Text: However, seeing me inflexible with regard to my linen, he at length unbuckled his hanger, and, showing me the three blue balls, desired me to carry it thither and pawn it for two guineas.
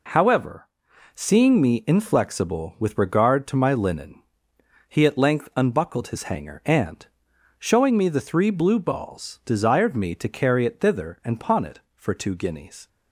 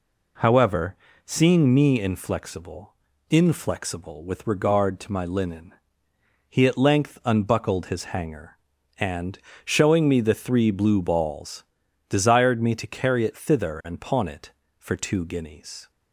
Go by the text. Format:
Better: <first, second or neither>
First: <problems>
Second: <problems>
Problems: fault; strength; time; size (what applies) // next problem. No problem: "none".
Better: first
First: none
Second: says "inflexible" twice; at 3.2 s